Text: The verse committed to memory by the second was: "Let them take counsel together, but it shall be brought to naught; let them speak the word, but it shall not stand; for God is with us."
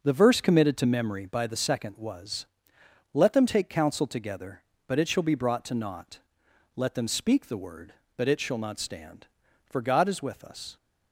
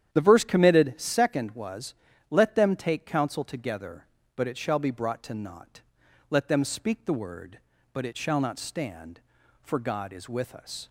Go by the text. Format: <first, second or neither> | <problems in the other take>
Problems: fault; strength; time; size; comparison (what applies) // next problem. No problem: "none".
first | starts louder than the rest; strong; until 1.1 s; 10 dB // skips "to memory by the"; at 0.9 s